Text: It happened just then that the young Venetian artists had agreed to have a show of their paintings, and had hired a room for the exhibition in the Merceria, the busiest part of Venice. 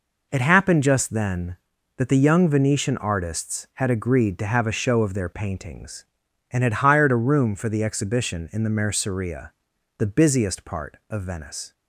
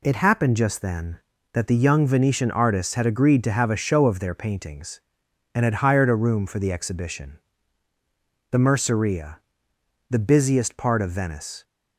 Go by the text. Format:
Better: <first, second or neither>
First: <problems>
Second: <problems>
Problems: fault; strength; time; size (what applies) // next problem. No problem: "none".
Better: first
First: none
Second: skips "in"; at 7.9 s